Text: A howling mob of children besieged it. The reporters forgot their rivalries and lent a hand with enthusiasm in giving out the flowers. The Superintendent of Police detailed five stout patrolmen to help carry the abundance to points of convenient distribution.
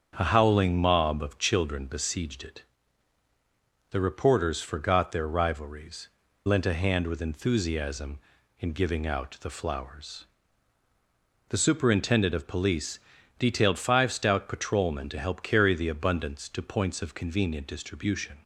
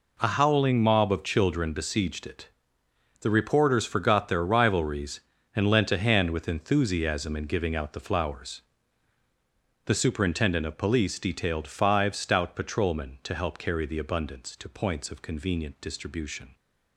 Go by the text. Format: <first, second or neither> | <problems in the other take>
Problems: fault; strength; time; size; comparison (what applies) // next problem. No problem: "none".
second | starts louder than the rest; strong; until 1.1 s; 7.5 dB // skips "and"; at 6.2 s // pauses between "Police" and "detailed"; at 13.0 s; 0.38 s long